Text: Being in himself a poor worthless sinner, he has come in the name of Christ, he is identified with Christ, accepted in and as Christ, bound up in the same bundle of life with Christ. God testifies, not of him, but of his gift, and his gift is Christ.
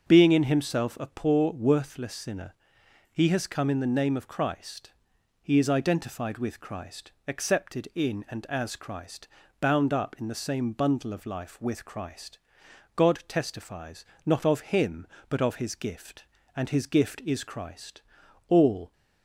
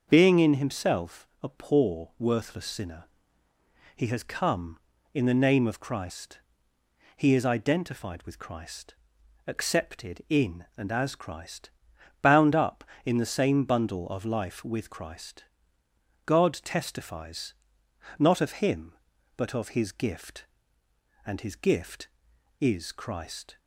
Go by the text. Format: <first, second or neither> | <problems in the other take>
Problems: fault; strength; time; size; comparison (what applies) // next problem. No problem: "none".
second | starts louder than the rest; until 1.1 s; 6.5 dB; also in the second // goes on to say "All"; slight; from 18.4 s on; 0.44 s long